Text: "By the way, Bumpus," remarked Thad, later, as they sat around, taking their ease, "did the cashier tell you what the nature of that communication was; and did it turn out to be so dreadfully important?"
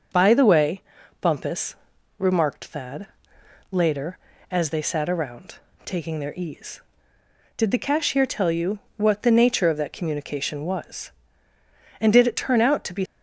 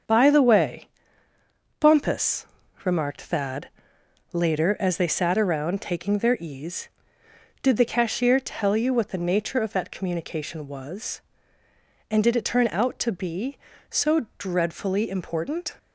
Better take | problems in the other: second | starts louder than the rest; noticeable; until 1.5 s; 6 dB; also in the second // pauses between "you" and "what"; slight; at 8.7 s; 0.16 s long // stops before "so dreadfully important"; at 13.0 s

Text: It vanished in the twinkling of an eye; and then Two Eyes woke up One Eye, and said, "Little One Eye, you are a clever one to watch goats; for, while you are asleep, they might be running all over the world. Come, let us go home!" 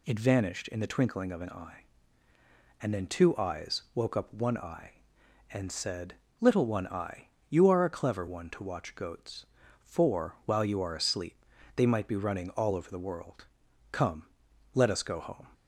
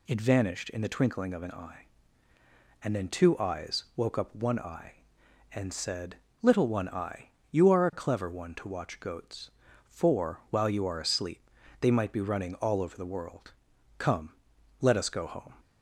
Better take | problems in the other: neither | none

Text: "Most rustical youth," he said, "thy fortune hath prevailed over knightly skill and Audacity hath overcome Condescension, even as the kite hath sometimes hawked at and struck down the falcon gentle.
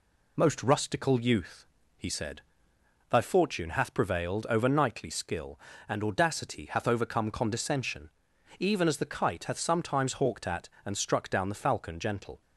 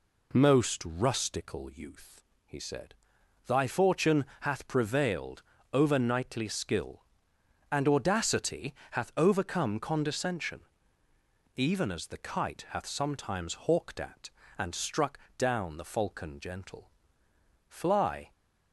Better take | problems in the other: first | pauses between "fortune" and "hath"; slight; at 4.2 s; 0.18 s long // pauses between "prevailed" and "over"; slight; at 5.4 s; 0.32 s long // pauses between "Audacity" and "hath"; slight; at 8.7 s; 0.18 s long // pauses between "struck" and "down"; slight; at 15.1 s; 0.18 s long // goes on to say "Fly"; noticeable; from 17.6 s on; 0.64 s long

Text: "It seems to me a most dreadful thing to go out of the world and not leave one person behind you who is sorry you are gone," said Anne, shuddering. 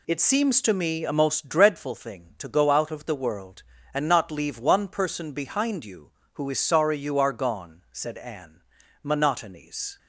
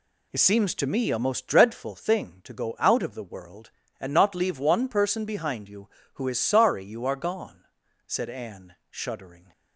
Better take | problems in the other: second | says "monotonies" for "shuddering"; at 9.0 s

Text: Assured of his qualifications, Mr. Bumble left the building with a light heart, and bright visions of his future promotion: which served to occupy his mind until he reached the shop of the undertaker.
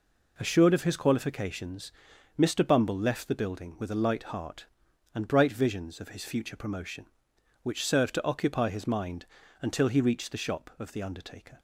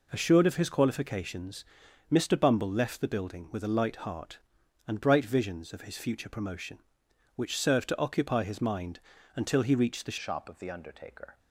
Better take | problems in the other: first | pauses between "mind" and "until"; slight; at 8.9 s; 0.36 s long; slight in the first // changes voice at "shop"; from 10.2 s on; 1.1 s long

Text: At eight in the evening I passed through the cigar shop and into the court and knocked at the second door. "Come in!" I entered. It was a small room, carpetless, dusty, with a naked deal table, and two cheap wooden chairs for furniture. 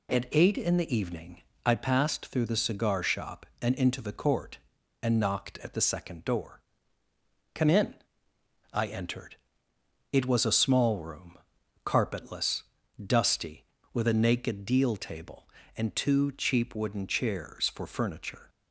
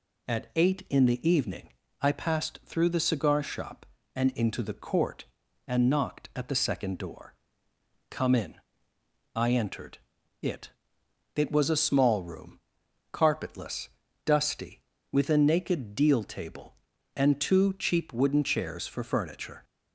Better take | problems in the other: first | pauses between "evening" and "I"; slight; at 1.6 s; 0.32 s long; slight in the first // says "It" twice; at 11.3 s

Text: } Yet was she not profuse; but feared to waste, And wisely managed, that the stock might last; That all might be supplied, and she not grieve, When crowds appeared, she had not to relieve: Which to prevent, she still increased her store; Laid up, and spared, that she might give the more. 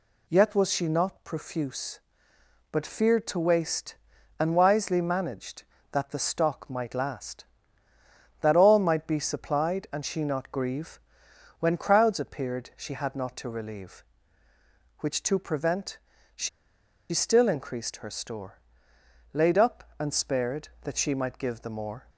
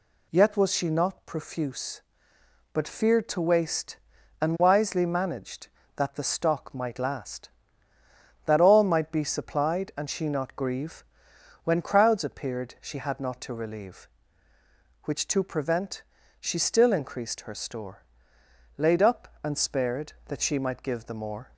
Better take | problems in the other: second | pauses between "she" and "still"; noticeable; at 16.4 s; 0.62 s long

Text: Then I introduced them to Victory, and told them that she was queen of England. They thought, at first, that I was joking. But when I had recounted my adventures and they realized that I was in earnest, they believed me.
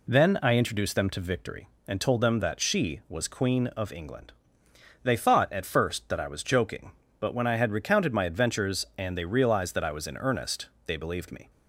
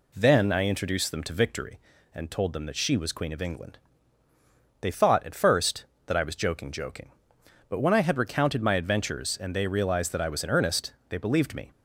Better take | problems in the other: first | says "joking" twice; at 6.7 s

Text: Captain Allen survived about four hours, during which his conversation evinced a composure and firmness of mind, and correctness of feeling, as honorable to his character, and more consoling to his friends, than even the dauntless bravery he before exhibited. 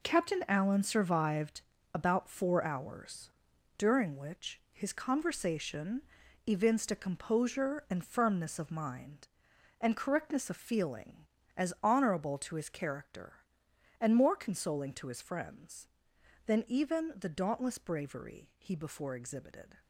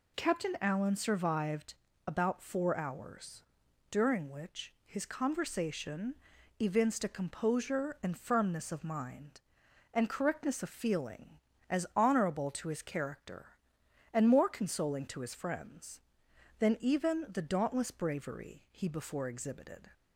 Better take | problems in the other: second | gets quieter; strong; throughout; 9.5 dB // pauses between "survived" and "about"; slight; at 1.6 s; 0.34 s long; slight in the second // pauses between "conversation" and "evinced"; at 6.0 s; 0.42 s long; also in the second

